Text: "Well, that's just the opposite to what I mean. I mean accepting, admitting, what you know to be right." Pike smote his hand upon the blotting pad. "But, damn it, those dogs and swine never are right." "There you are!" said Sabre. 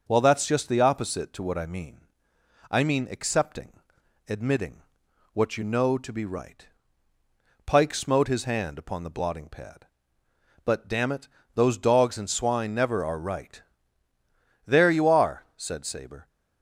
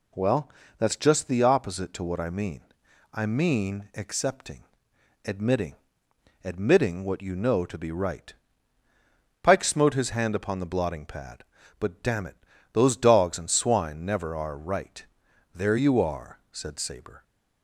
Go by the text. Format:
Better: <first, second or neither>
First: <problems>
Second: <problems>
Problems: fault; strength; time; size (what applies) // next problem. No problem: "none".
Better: first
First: none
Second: says "admitting" twice; at 6.4 s